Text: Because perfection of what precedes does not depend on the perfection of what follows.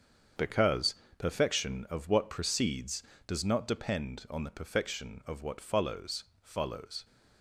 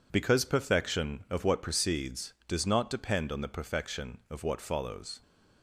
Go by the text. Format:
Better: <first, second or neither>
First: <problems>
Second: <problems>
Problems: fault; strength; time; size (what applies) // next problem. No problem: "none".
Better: second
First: starts louder than the rest; strong; until 1.6 s; 7 dB // pauses between "Because" and "perfection"; slight; at 0.9 s; 0.24 s long // says "follows" twice; at 6.4 s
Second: none